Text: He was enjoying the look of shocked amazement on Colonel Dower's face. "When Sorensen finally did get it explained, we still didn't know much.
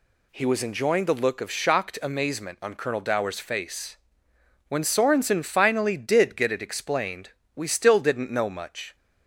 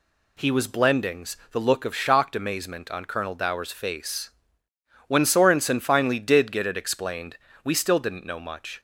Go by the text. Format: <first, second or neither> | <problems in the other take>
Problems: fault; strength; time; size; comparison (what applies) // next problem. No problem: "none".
first | says "blendings" for "enjoying"; at 0.6 s